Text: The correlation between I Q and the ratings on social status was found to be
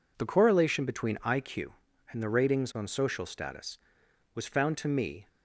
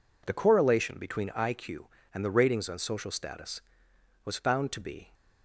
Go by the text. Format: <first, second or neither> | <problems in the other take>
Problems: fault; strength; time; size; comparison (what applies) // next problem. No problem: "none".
second | says "me" for "be"; at 4.8 s